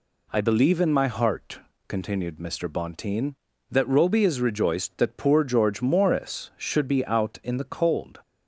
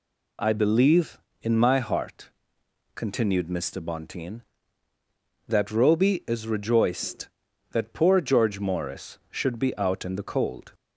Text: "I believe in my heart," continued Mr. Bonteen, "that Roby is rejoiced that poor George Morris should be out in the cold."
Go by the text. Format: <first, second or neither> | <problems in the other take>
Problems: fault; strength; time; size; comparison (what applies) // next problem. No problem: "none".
neither | none